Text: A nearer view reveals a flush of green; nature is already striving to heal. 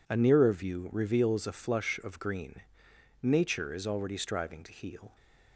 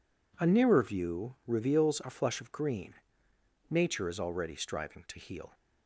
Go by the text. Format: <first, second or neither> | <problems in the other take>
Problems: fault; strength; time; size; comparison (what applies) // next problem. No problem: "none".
neither | none